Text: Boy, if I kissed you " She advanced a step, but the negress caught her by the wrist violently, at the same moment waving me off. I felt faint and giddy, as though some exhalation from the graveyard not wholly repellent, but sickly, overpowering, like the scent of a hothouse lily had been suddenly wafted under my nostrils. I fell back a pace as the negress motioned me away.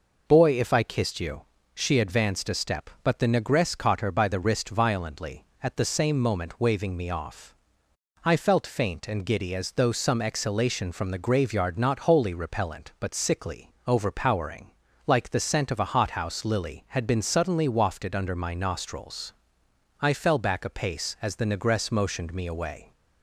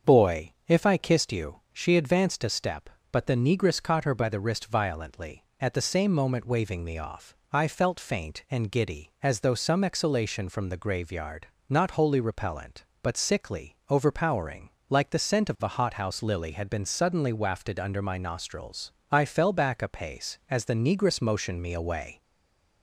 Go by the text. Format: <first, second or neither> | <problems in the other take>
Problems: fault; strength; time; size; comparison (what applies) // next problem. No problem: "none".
first | starts louder than the rest; until 1.1 s; 7 dB // pauses between "graveyard" and "not"; slight; at 11.4 s; 0.22 s long // stays silent after the last word; slight; from 22.2 s on; 0.6 s long